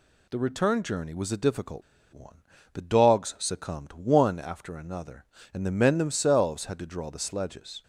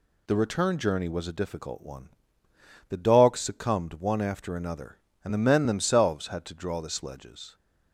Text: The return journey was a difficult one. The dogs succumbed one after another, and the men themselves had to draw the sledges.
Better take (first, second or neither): second